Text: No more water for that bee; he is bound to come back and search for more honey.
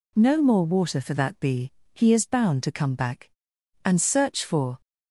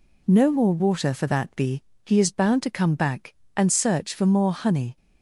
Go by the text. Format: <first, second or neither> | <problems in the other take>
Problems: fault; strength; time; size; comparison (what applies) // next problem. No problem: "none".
second | stops before "more honey"; at 4.8 s